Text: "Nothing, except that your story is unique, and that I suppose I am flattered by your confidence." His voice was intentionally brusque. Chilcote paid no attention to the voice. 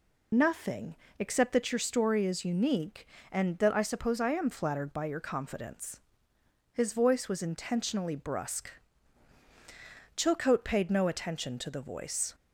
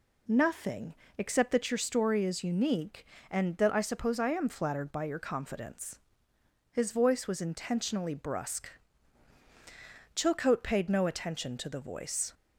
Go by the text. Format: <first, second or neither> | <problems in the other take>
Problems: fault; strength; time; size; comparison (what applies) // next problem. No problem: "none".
second | loses the start of "Nothing"; at 0.3 s; 35 ms